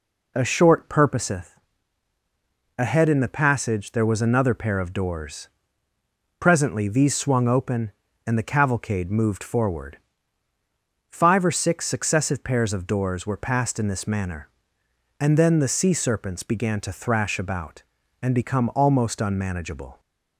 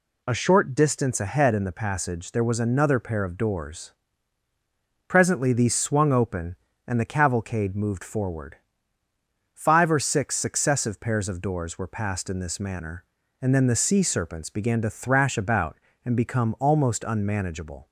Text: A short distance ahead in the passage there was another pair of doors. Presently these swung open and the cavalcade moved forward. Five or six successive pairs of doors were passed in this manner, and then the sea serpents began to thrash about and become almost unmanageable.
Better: second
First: says "purposeth" for "distance"; at 0.8 s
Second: none

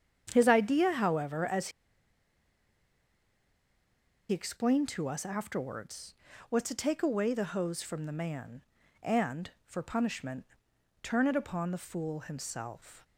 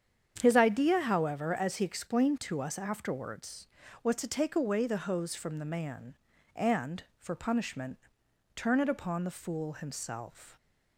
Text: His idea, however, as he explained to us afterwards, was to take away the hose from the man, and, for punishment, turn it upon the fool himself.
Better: second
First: starts louder than the rest; strong; until 1.3 s; 8.5 dB // pauses between "as" and "he"; strong; at 1.6 s; 2.6 s long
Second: starts louder than the rest; strong; until 1.4 s; 8.5 dB

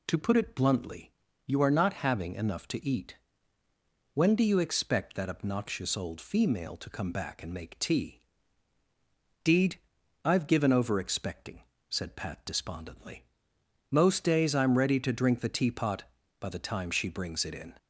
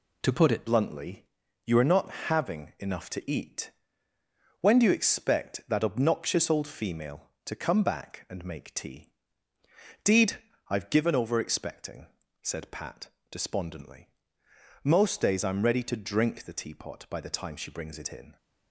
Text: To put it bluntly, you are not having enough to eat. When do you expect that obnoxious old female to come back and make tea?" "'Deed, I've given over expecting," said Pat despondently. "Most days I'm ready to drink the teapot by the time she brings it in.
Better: first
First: none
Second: changes voice at "bluntly"; from 0.6 s on; 17.7 s long // pauses between "not" and "having"; slight; at 2.1 s; 0.16 s long // pauses between "Pat" and "despondently"; slight; at 13.0 s; 0.22 s long

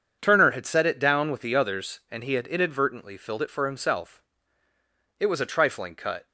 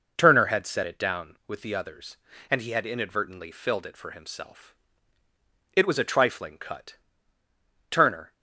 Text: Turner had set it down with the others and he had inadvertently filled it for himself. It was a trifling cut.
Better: first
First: none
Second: goes on to say "Turner"; slight; from 7.9 s on; 0.42 s long

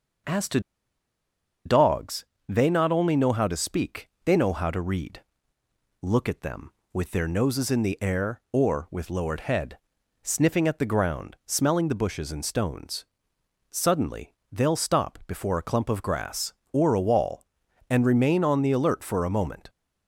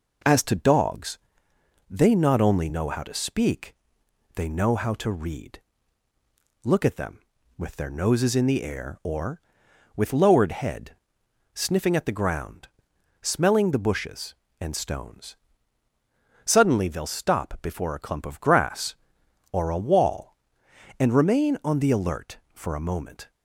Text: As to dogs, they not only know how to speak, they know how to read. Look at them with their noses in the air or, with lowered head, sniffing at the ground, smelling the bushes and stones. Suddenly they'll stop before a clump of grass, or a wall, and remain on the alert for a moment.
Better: second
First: pauses between "to" and "dogs"; at 0.6 s; 1.0 s long // pauses between "Suddenly" and "they'll"; slight; at 14.3 s; 0.18 s long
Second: none

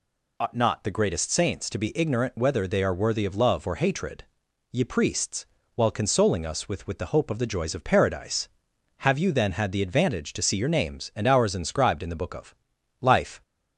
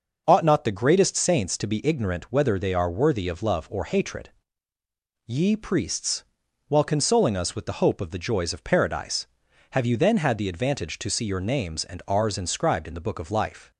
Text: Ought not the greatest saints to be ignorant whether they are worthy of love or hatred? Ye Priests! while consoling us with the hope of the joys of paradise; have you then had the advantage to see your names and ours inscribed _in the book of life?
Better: second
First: says "with" twice; at 6.8 s // pauses between "of" and "life"; at 12.5 s; 0.44 s long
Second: none

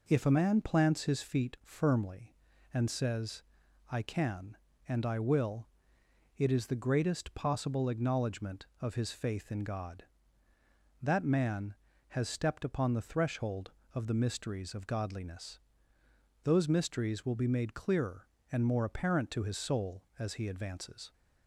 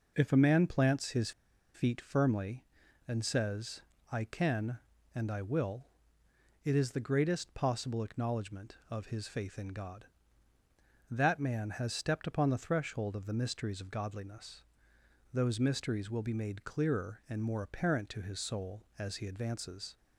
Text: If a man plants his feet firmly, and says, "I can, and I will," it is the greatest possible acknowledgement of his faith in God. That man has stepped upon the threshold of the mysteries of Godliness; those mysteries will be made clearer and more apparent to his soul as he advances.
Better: first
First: none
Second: pauses between "his" and "feet"; at 1.3 s; 0.42 s long

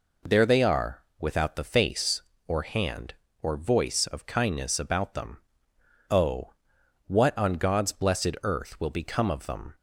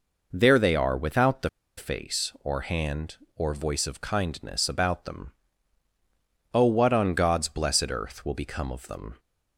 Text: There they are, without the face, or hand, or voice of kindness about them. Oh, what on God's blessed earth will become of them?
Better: first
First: none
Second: pauses between "the" and "face"; slight; at 1.4 s; 0.28 s long

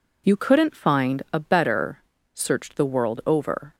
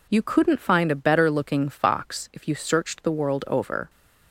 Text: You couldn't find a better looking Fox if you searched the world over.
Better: second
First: skips "looking Fox if you"; at 2.1 s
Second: none

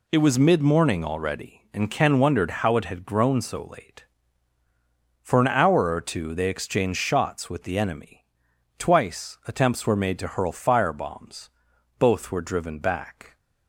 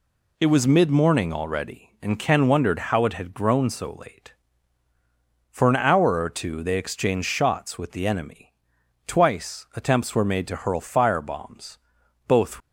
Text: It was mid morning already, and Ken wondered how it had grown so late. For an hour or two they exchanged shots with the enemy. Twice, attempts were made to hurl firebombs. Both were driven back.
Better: first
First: none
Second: stops before "were driven back"; at 12.6 s

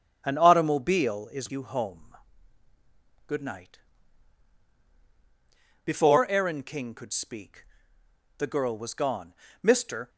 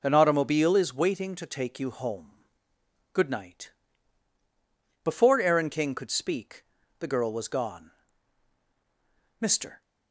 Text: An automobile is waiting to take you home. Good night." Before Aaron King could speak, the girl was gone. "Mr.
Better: second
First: starts louder than the rest; strong; until 1.2 s; 9 dB // skips "waiting to take"; at 1.5 s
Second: none

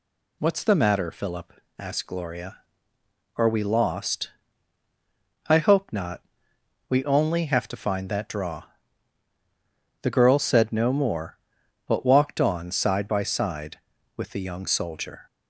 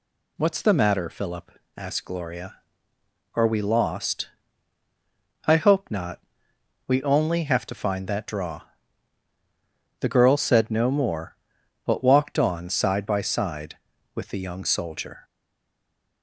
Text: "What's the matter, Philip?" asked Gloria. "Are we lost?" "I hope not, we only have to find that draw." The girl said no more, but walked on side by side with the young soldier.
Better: first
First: none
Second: stays silent after the last word; from 15.2 s on; 1.0 s long

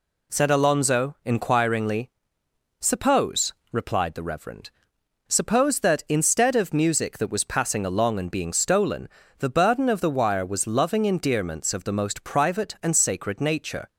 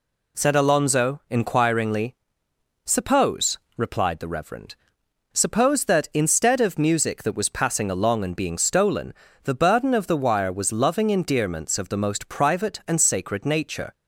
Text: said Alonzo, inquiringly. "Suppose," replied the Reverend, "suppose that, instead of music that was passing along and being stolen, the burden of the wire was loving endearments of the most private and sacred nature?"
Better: neither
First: none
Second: none

